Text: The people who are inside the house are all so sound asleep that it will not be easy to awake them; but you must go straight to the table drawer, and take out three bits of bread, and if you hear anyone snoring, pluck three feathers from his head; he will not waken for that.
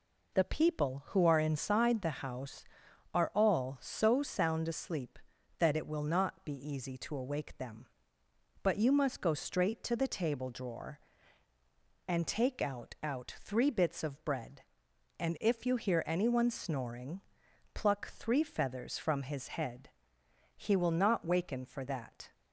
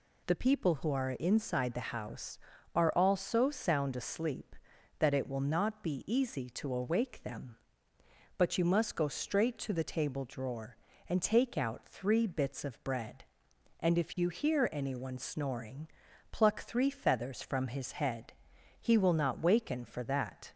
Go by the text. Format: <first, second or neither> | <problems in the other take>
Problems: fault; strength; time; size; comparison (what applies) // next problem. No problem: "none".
second | says "out" twice; at 13.0 s